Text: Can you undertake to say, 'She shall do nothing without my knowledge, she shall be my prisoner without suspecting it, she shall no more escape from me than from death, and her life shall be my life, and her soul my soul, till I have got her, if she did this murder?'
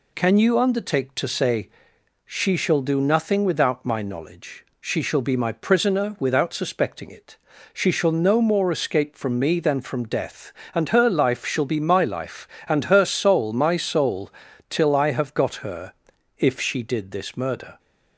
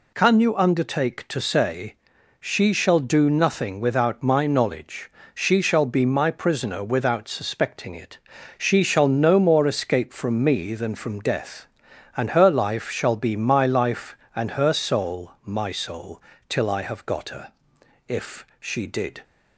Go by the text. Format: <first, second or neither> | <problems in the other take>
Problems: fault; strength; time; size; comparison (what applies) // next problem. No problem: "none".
first | stops before "this murder"; at 19.2 s